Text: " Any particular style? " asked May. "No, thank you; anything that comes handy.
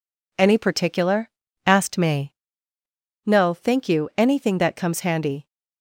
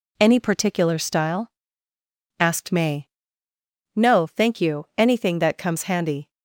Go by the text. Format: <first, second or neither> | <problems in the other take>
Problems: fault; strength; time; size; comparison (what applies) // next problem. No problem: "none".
second | skips "style"; at 1.3 s